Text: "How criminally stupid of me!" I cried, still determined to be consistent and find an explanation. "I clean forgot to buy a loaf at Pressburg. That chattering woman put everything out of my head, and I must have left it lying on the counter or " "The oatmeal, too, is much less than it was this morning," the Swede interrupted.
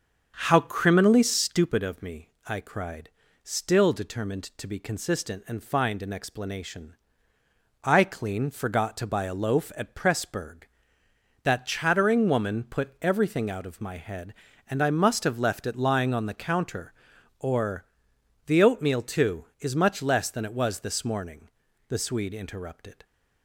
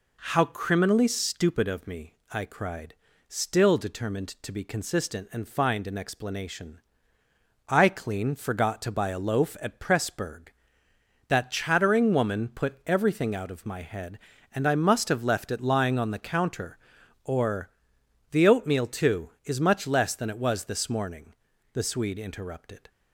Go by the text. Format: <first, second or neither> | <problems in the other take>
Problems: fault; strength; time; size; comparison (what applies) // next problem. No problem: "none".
second | starts louder than the rest; until 1.7 s; 7 dB